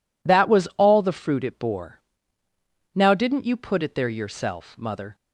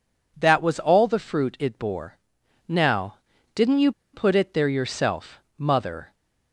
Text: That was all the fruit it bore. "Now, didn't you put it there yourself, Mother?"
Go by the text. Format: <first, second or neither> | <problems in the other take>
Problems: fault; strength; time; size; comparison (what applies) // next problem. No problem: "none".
first | pauses between "you" and "put"; slight; at 3.9 s; 0.21 s long